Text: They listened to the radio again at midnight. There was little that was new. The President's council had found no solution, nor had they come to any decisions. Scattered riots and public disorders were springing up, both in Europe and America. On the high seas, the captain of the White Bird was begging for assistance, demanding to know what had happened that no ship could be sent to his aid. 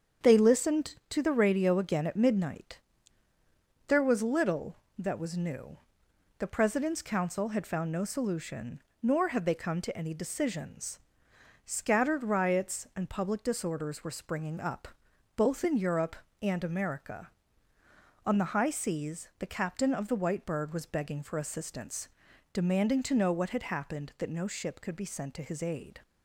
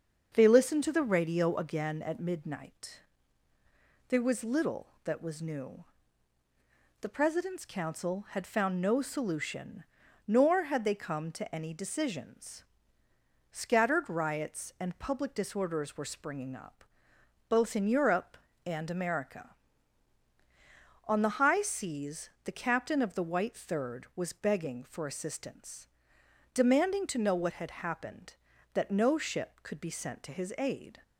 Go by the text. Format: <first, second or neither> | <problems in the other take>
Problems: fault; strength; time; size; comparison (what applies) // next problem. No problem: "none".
first | starts louder than the rest; until 1.3 s; 6.5 dB; strong in the first // says "Third" for "Bird"; at 23.5 s